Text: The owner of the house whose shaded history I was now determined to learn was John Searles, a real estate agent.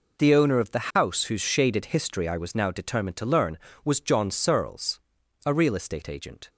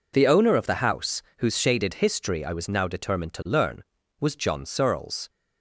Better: first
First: none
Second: pauses between "house" and "whose"; slight; at 1.2 s; 0.16 s long // stops before "a real estate agent"; at 5.2 s

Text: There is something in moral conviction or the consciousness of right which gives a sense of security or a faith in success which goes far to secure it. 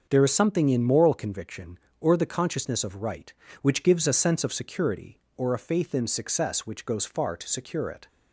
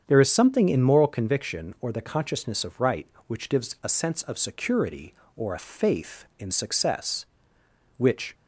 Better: first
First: starts louder than the rest; until 1.1 s; 6.5 dB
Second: starts louder than the rest; strong; until 1.0 s; 8 dB // stops before "goes far to secure it"; at 8.3 s

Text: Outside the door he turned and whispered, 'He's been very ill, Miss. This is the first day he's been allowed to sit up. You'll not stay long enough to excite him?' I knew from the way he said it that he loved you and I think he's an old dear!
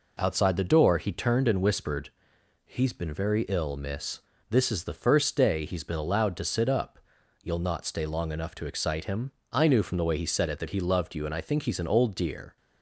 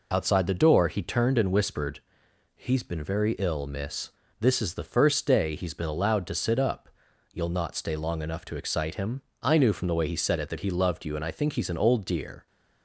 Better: first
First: none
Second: loses the start of "Outside"; at 0.1 s; 35 ms

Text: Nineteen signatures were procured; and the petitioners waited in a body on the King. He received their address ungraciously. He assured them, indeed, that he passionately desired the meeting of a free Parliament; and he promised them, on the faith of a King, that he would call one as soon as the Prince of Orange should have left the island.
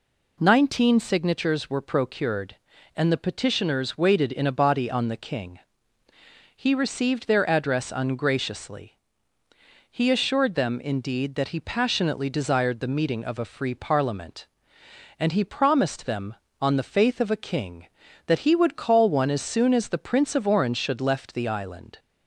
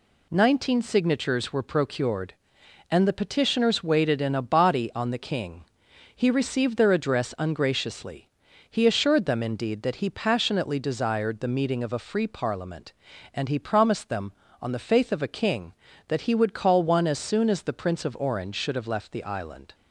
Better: second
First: skips "have"; at 21.0 s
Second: none

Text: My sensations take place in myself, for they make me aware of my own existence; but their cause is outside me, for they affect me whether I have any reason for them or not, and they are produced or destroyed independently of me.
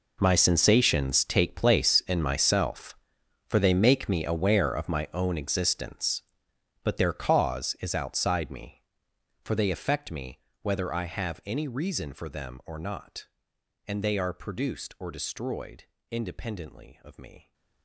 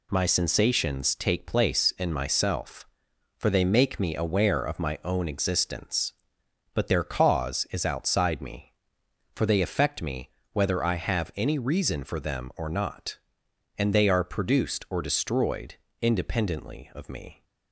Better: second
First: gets quieter; strong; throughout; 17 dB // pauses between "me" and "whether"; slight; at 10.3 s; 0.22 s long // pauses between "destroyed" and "independently"; slight; at 15.8 s; 0.26 s long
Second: pauses between "me" and "whether"; slight; at 10.2 s; 0.22 s long // pauses between "destroyed" and "independently"; slight; at 15.7 s; 0.26 s long

